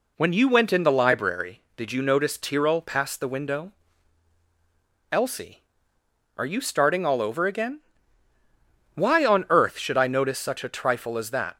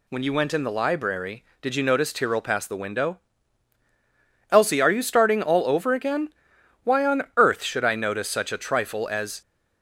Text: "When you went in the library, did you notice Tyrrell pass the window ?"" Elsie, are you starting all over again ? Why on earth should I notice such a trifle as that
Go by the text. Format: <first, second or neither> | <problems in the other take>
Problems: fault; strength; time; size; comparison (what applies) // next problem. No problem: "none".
first | stops before "that"; at 9.4 s